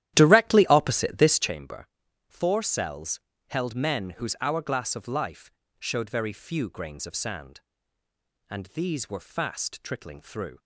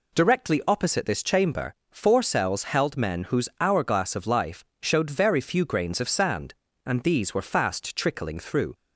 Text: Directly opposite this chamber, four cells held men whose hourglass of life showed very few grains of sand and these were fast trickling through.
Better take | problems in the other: second | starts louder than the rest; strong; until 1.5 s; 12.5 dB // pauses between "cells" and "held"; slight; at 3.1 s; 0.30 s long // pauses between "life" and "showed"; slight; at 5.5 s; 0.30 s long; slight in the second

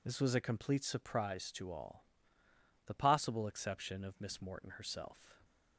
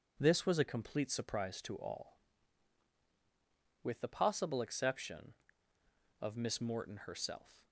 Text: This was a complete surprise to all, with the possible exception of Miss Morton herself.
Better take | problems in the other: second | skips "with"; at 2.4 s

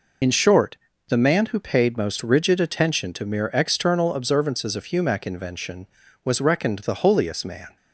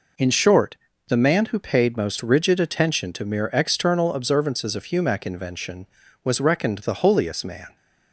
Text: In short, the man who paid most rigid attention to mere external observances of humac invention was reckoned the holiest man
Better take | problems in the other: second | loses the start of "In"; at 0.2 s; 40 ms

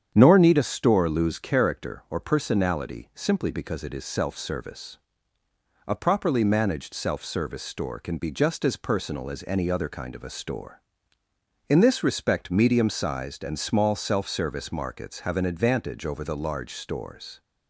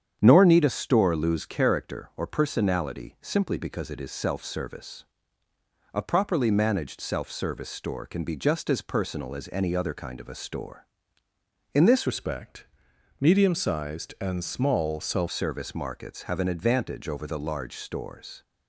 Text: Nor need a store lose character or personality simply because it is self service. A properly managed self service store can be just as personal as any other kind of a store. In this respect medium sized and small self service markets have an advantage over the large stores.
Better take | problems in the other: first | starts louder than the rest; strong; until 1.2 s; 8.5 dB; strong in the first // changes voice from "respect" to "self"; from 12.0 to 15.2 s; 3.2 s long // pauses between "respect" and "medium"; noticeable; at 12.6 s; 0.54 s long

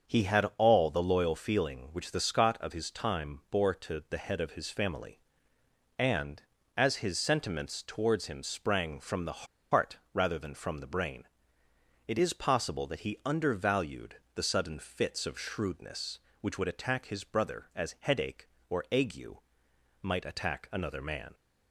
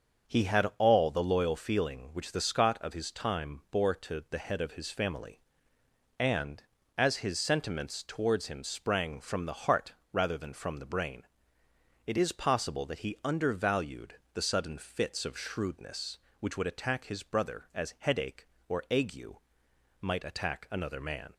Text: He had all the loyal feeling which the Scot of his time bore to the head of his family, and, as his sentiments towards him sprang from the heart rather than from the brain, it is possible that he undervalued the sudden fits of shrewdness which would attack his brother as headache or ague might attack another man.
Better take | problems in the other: second | starts louder than the rest; until 1.1 s; 6.5 dB; also in the second // pauses between "the" and "heart"; slight; at 9.4 s; 0.26 s long // pauses between "heart" and "rather"; slight; at 9.9 s; 0.16 s long; slight in the second // pauses between "undervalued" and "the"; slight; at 14.1 s; 0.20 s long; slight in the second // pauses between "ague" and "might"; noticeable; at 19.3 s; 0.66 s long; noticeable in the second

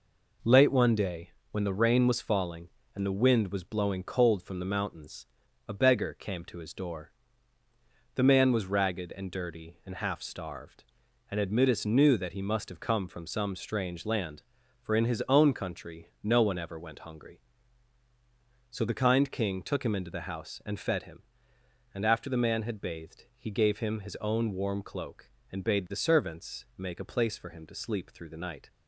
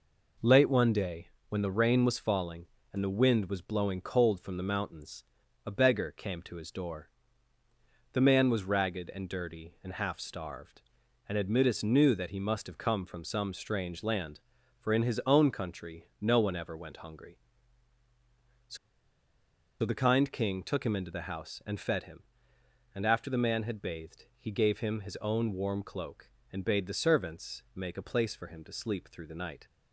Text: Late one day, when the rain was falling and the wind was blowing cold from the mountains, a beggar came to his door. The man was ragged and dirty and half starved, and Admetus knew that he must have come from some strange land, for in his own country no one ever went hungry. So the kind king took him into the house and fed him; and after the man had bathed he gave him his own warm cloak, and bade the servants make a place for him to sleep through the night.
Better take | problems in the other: first | pauses between "So" and "the"; at 18.7 s; 1.0 s long

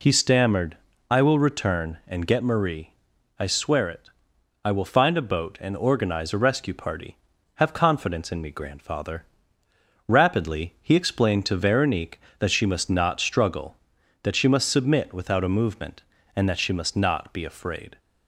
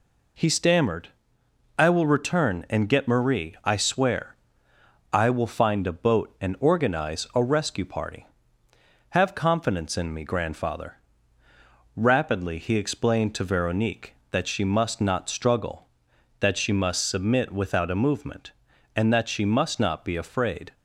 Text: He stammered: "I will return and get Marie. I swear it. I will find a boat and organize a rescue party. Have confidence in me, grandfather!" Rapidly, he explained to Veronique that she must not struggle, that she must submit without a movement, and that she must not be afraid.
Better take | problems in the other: first | skips "it"; at 4.7 s

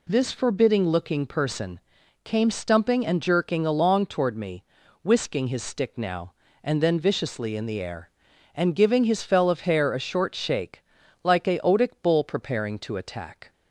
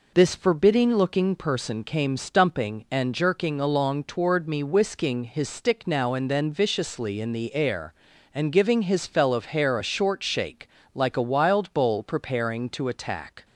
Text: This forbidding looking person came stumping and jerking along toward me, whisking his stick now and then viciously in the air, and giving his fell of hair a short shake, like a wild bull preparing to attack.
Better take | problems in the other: second | pauses between "person" and "came"; at 1.7 s; 0.44 s long // says "otic" for "wild"; at 11.5 s

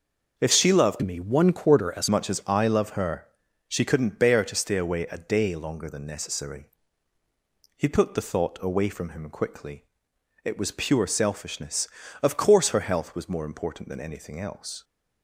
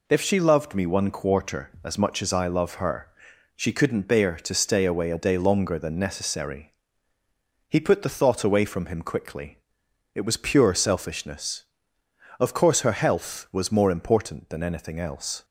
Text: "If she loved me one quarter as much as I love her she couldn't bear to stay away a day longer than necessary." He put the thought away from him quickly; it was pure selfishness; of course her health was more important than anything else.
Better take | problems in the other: second | starts louder than the rest; until 1.4 s; 6 dB // changes voice from "me" to "as"; from 1.0 to 2.0 s; 1.0 s long // pauses between "her" and "she"; at 3.2 s; 0.42 s long; noticeable in the second

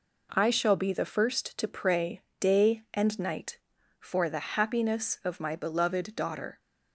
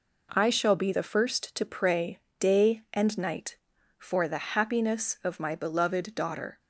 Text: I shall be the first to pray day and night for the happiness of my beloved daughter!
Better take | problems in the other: neither | pauses between "pray" and "day"; slight; the same in both

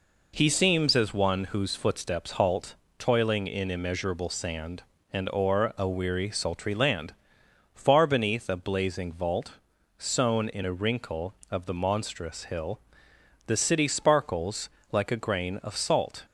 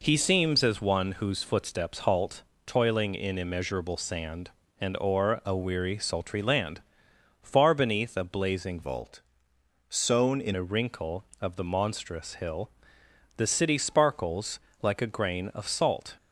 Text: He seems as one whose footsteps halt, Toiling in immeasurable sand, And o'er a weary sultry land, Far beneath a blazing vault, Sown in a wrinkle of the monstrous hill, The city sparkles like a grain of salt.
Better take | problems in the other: first | changes voice from "vault" to "in"; from 8.8 to 10.5 s; 1.7 s long // pauses between "sparkles" and "like"; slight; at 14.5 s; 0.22 s long; slight in the first

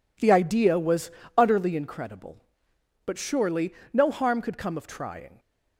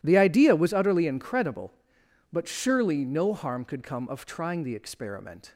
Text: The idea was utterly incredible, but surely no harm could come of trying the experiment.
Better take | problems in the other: second | pauses between "was" and "utterly"; slight; at 1.1 s; 0.26 s long // pauses between "surely" and "no"; slight; at 3.7 s; 0.20 s long // stops before "the experiment"; at 5.3 s

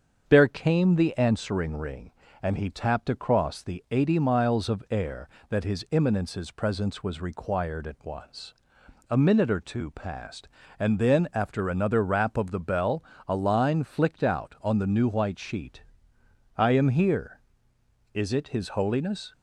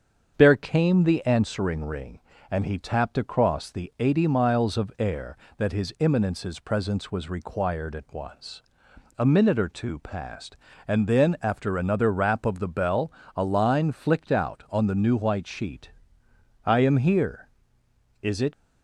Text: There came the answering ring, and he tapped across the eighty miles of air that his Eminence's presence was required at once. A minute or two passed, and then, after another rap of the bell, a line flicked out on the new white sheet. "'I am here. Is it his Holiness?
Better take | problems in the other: first | starts louder than the rest; strong; until 1.3 s; 7 dB; also in the first // stops before "his Holiness"; at 18.5 s

